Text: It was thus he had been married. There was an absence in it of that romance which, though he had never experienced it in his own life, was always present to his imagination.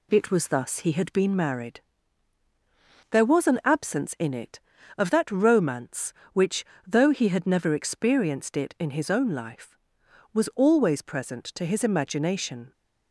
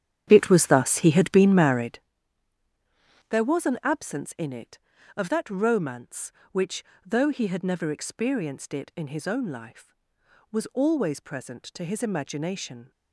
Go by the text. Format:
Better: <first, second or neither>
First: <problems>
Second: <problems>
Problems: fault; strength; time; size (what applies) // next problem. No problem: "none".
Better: first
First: none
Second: starts louder than the rest; strong; until 2.1 s; 9.5 dB